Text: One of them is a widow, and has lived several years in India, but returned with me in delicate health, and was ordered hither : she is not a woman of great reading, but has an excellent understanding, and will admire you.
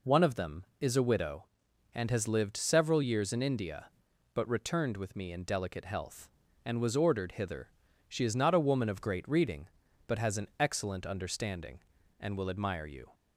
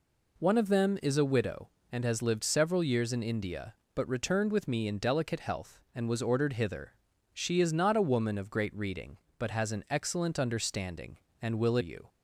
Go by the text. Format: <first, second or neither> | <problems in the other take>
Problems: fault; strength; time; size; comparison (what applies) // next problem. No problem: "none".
first | skips "admire"; at 11.7 s